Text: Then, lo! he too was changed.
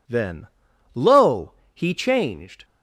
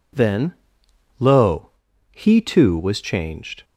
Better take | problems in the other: second | skips "too was"; at 1.9 s

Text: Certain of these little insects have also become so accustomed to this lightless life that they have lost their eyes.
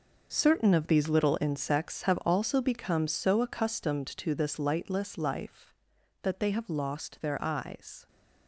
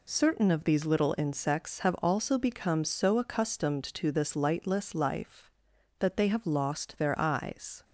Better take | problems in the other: second | gets quieter; strong; throughout; 13 dB

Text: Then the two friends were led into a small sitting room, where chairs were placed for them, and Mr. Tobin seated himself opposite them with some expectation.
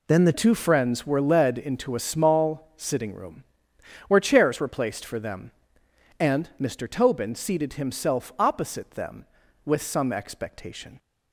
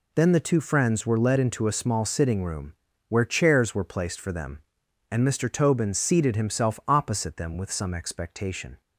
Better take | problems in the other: second | changes voice at "two"; from 0.3 s on; 10.6 s long

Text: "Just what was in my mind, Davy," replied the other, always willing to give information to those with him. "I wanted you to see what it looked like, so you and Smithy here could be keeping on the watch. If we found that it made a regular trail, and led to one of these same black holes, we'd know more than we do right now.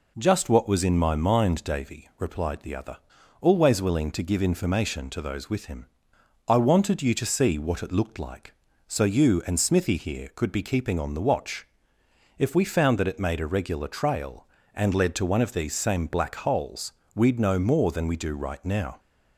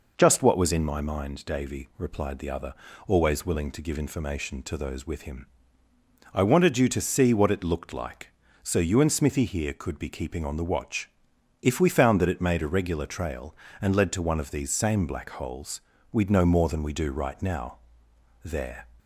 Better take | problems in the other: first | goes on to say "There"; slight; from 18.4 s on; 0.44 s long

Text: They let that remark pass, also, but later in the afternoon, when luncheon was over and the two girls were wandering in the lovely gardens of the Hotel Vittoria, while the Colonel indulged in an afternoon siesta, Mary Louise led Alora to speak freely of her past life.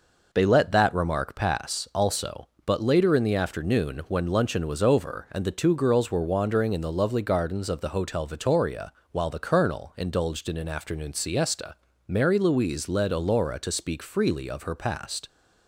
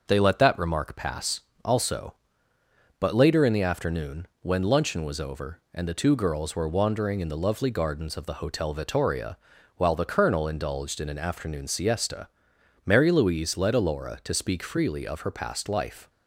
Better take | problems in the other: second | stops before "life"; at 15.2 s

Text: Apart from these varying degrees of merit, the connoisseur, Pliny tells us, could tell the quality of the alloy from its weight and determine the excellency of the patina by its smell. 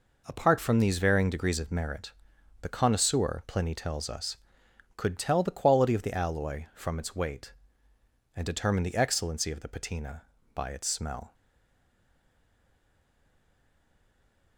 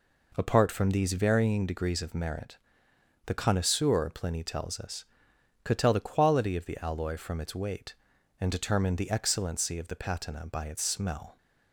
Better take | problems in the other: second | stays silent after the last word; strong; from 11.3 s on; 3.2 s long

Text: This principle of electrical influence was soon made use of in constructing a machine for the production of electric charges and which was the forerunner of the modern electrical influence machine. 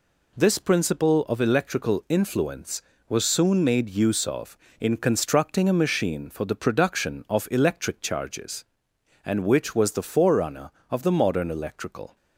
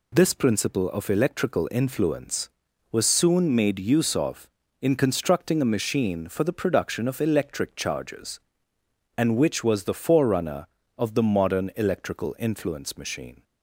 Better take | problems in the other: second | stops before "influence machine"; at 12.1 s

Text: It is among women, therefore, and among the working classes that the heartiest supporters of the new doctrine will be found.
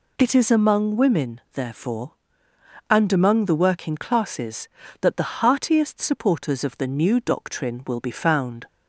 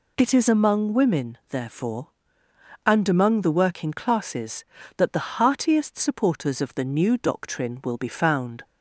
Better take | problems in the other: neither | none

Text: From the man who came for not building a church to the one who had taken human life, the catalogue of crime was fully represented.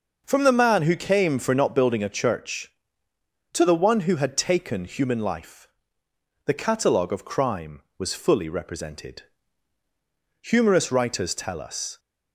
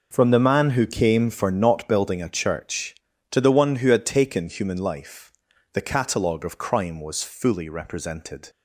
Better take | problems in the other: second | goes on to say "Humorous writers tell us"; from 10.4 s on; 1.5 s long

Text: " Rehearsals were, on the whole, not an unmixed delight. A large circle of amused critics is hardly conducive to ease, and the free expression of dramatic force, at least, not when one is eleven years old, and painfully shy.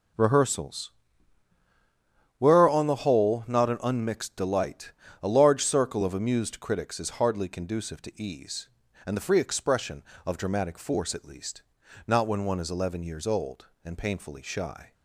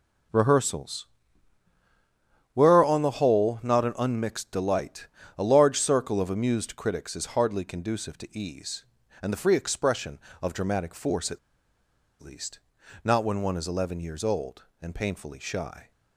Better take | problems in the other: first | pauses between "at" and "least"; noticeable; at 11.3 s; 0.83 s long

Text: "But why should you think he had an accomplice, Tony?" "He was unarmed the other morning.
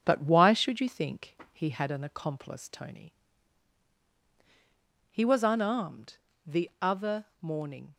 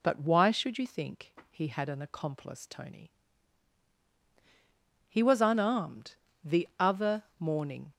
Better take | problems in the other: second | gets quieter; throughout; 3.5 dB // pauses between "think" and "he"; slight; at 1.3 s; 0.16 s long; slight in the second // pauses between "unarmed" and "the"; slight; at 6.1 s; 0.28 s long; slight in the second

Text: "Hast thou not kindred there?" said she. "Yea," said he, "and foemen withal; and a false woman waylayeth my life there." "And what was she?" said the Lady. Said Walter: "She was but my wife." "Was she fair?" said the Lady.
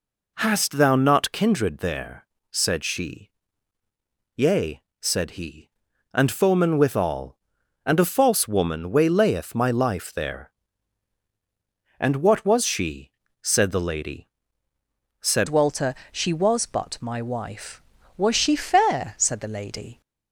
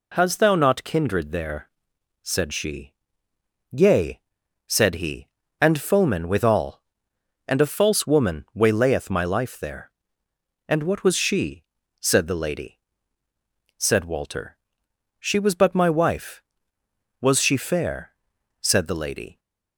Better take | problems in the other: second | changes voice at "Walter"; from 15.4 s on; 4.6 s long

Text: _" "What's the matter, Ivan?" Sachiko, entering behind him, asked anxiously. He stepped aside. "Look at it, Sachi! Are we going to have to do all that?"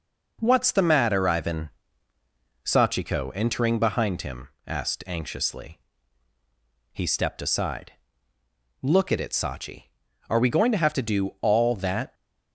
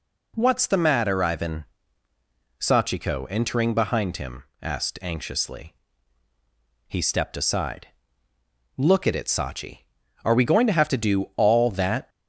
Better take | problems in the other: second | gets quieter; slight; throughout; 3.5 dB

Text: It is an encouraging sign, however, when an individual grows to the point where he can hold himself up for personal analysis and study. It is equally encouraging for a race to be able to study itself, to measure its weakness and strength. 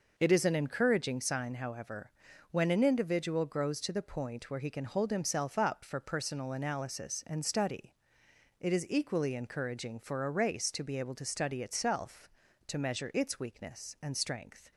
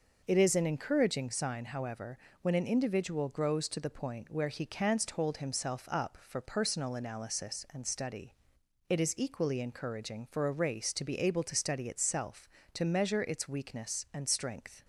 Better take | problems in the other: first | says "canst" for "can"; at 4.6 s

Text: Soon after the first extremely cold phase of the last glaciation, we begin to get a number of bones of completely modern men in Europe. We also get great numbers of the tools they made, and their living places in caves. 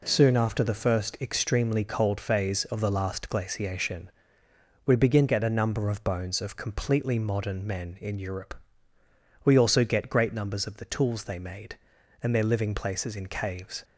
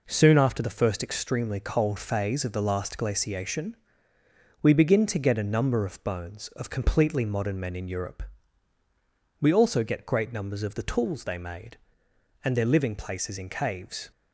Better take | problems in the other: second | skips "to"; at 5.2 s

